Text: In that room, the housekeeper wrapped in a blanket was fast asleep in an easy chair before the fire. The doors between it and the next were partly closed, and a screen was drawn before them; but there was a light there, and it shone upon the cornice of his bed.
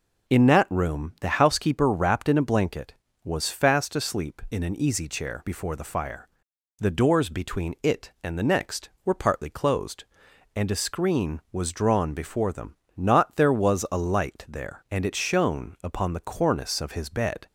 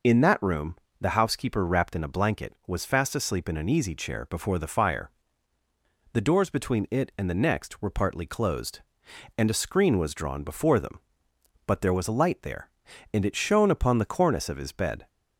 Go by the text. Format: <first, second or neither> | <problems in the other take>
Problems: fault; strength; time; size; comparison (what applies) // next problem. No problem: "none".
second | says "not" for "but"; at 12.9 s